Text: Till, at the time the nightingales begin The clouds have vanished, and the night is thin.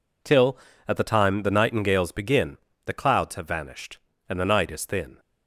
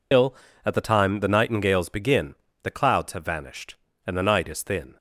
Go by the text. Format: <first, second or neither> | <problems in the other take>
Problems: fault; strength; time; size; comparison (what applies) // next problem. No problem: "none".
first | loses the start of "Till"; at 0.1 s; 105 ms // pauses between "begin" and "The"; slight; at 2.3 s; 0.26 s long; slight in the first